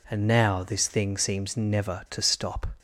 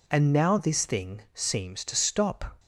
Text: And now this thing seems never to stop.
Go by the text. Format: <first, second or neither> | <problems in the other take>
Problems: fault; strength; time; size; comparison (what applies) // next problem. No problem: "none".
first | skips "never"; at 1.8 s